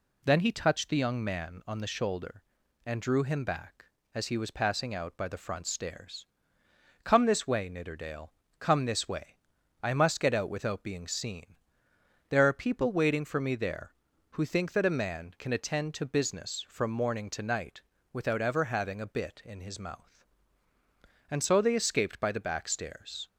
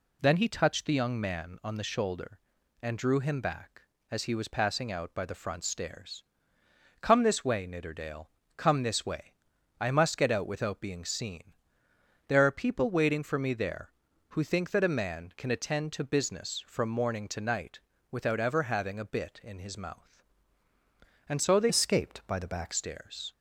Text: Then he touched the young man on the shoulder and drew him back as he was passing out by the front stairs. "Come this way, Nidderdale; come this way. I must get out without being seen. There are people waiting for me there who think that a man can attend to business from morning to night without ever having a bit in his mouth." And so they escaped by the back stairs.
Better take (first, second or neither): first